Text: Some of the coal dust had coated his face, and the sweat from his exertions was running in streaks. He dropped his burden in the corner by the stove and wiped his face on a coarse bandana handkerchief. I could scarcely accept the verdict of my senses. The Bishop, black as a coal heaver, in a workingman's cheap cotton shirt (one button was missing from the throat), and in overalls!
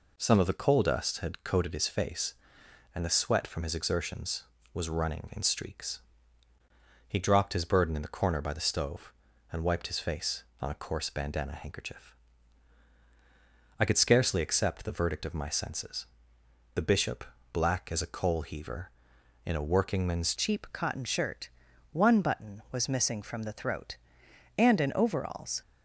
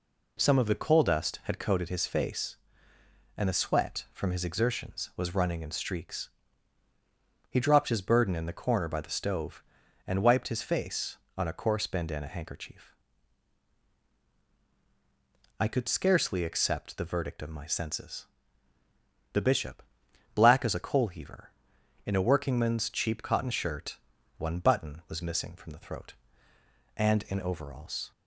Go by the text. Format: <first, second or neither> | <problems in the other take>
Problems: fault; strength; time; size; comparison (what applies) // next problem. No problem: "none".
second | changes voice at "cheap"; from 20.3 s on; 5.3 s long